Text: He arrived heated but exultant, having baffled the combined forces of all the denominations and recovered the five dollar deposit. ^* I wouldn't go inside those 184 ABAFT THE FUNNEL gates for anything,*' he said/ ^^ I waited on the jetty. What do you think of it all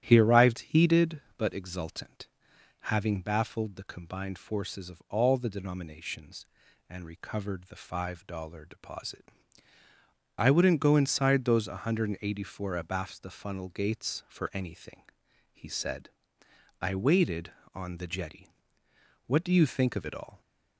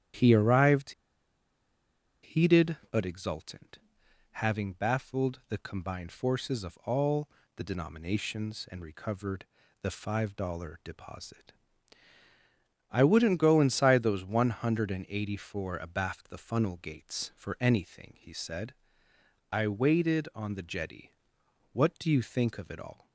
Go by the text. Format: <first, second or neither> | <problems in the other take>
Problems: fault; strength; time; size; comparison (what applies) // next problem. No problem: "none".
first | starts louder than the rest; strong; until 2.4 s; 10 dB; strong in the first // pauses between "arrived" and "heated"; strong; at 0.9 s; 1.3 s long // pauses between "all" and "the"; slight; at 7.2 s; 0.28 s long // pauses between "recovered" and "the"; at 9.4 s; 0.38 s long